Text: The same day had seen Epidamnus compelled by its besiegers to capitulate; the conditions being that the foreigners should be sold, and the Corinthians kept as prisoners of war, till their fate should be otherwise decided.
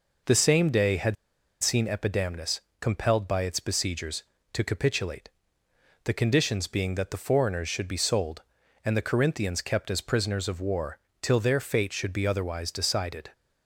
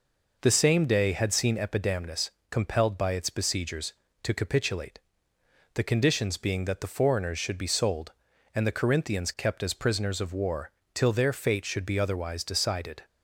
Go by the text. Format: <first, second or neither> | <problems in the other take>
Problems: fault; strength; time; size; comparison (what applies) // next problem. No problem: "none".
second | pauses between "had" and "seen"; noticeable; at 1.1 s; 0.48 s long // pauses between "Epidamnus" and "compelled"; slight; at 2.5 s; 0.20 s long; slight in the second